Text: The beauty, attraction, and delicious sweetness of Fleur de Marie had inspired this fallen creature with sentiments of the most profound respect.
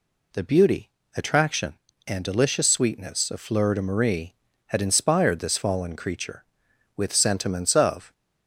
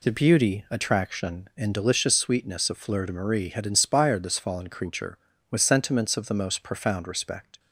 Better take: second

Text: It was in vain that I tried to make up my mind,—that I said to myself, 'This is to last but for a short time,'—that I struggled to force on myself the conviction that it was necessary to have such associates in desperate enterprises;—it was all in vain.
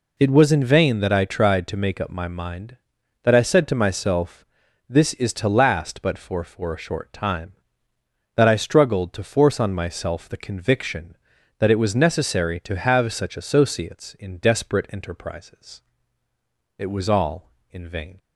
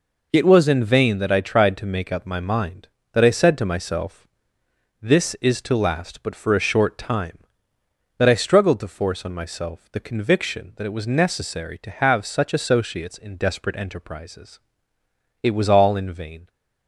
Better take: second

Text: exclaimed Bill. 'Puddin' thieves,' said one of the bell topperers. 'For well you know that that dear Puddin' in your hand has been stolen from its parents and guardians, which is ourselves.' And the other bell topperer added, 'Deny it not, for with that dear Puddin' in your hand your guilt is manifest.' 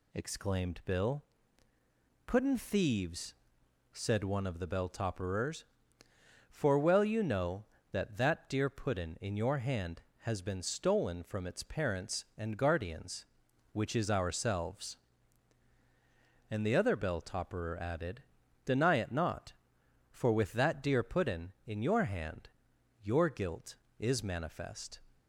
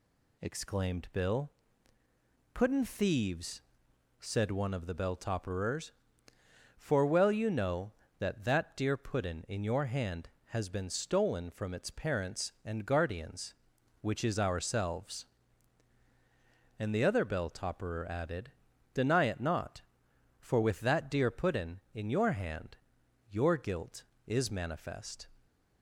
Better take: neither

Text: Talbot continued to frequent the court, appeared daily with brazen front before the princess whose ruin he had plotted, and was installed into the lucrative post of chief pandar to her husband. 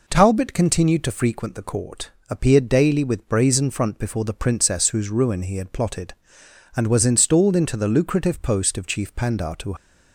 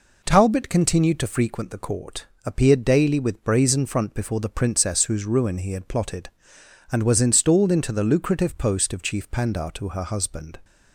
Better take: second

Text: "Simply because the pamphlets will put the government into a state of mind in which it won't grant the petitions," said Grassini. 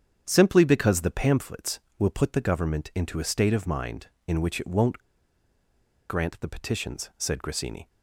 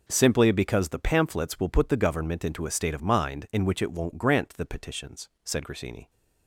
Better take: second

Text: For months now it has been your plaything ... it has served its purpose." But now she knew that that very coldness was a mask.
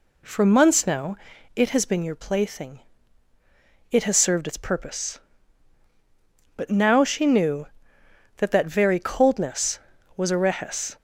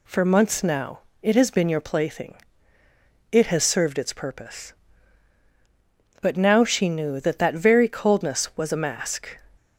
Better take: second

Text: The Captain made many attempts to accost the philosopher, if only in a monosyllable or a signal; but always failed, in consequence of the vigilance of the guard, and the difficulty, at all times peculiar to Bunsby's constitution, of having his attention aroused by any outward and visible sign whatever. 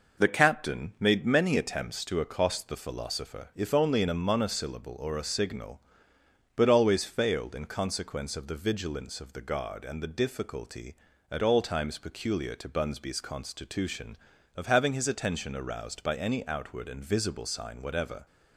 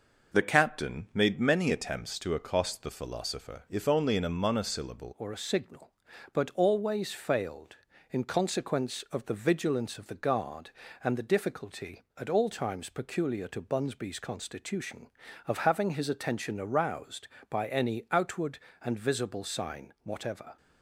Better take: first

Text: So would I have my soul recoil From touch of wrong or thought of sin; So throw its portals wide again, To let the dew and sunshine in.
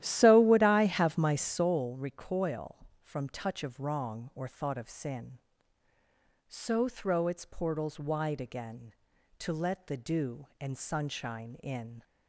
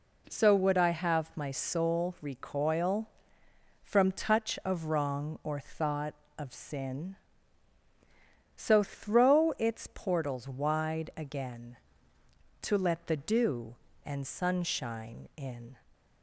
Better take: second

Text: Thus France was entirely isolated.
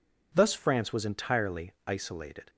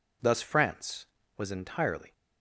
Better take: first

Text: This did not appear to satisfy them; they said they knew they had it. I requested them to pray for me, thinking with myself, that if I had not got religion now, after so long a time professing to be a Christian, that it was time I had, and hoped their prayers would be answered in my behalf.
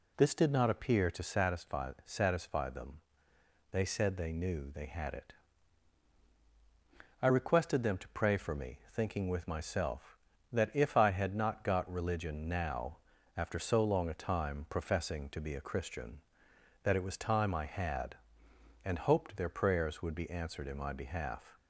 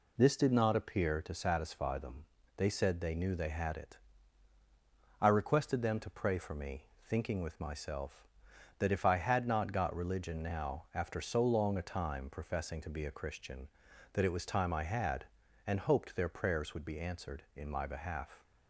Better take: second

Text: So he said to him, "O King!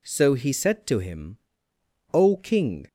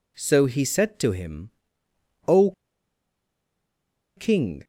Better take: first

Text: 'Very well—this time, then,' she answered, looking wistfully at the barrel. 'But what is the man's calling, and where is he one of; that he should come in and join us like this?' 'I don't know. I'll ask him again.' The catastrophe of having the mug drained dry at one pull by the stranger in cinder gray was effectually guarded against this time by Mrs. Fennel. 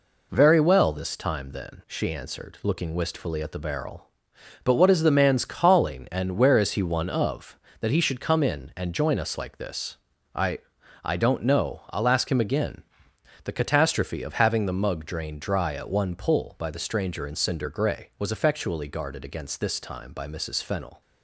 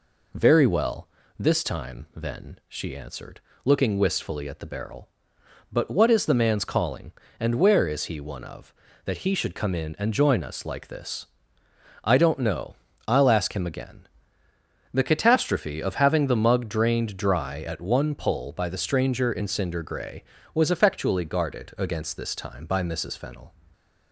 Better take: second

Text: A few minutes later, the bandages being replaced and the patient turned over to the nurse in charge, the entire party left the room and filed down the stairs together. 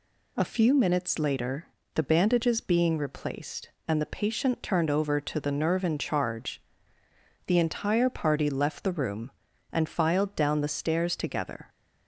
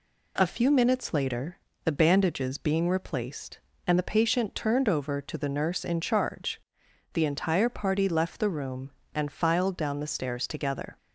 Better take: second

